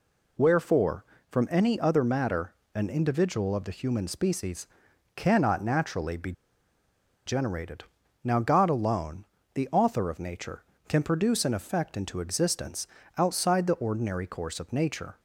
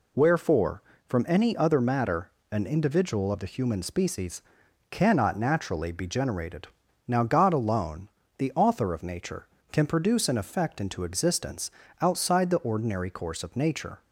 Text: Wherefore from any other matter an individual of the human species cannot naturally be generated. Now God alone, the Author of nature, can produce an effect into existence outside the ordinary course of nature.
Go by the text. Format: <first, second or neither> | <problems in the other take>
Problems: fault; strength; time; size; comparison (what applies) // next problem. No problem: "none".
second | pauses between "matter" and "an"; slight; at 2.5 s; 0.20 s long; slight in the second // pauses between "species" and "cannot"; noticeable; at 4.6 s; 0.48 s long; noticeable in the second // pauses between "be" and "generated"; noticeable; at 6.3 s; 0.94 s long // pauses between "existence" and "outside"; slight; at 12.8 s; 0.28 s long; slight in the second